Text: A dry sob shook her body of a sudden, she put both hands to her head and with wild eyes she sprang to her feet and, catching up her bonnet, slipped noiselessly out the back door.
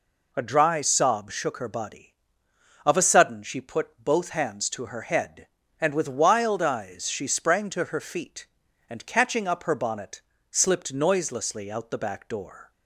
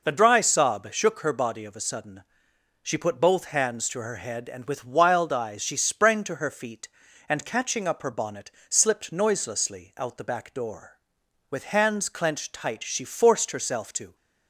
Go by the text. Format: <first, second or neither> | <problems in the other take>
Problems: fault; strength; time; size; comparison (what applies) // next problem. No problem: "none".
first | goes on to say "With hands clenched tight she forced herself to"; strong; from 11.5 s on; 2.6 s long